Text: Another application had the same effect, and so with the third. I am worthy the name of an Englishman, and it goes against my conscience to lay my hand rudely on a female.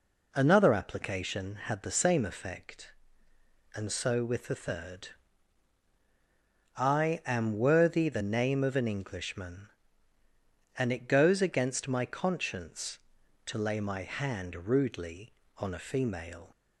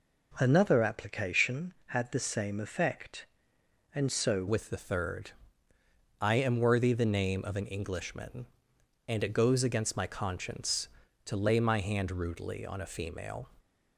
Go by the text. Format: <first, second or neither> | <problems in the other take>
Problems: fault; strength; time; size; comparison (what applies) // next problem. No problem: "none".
first | changes voice at "with"; from 4.4 s on; 9.0 s long